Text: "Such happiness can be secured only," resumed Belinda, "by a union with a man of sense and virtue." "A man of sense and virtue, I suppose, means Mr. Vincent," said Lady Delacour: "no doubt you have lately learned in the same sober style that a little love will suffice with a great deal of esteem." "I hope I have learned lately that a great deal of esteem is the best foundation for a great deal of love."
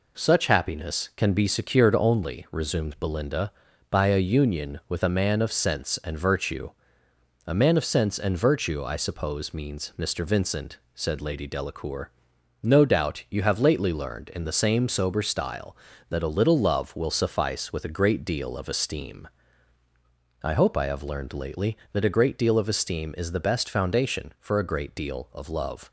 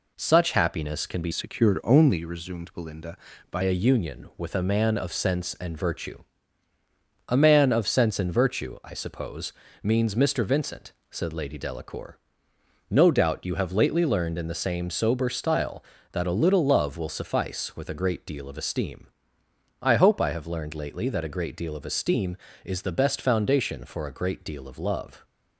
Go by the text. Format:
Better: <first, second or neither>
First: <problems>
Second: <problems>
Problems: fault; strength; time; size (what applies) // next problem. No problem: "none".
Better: first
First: none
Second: changes voice from "secured" to "by"; from 1.3 to 3.6 s; 2.3 s long